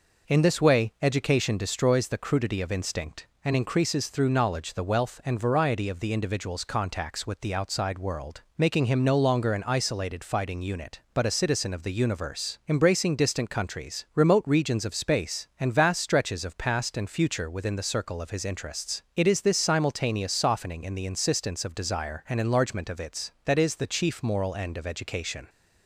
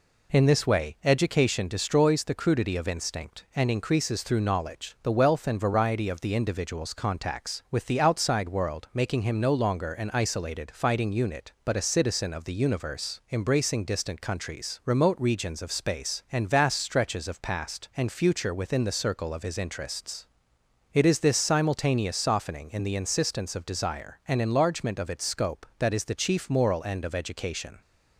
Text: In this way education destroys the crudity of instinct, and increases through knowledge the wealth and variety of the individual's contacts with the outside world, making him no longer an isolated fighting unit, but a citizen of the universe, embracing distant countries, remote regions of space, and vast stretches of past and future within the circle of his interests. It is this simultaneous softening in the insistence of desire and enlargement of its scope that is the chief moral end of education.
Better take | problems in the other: second | skips "scope"; at 23.3 s

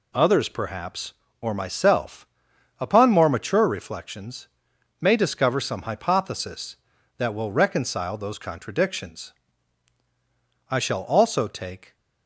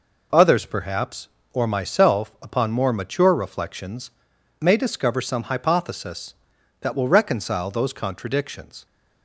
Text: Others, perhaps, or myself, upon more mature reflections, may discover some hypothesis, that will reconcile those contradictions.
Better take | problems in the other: second | goes on to say "I shall also take"; noticeable; from 10.7 s on; 1.2 s long

